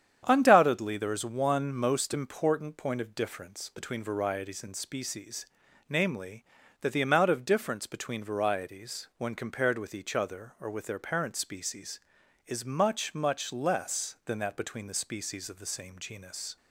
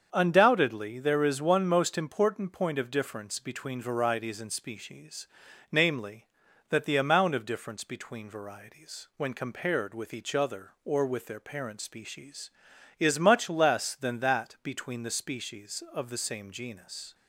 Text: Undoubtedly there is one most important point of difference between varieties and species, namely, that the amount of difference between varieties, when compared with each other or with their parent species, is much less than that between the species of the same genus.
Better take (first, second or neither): second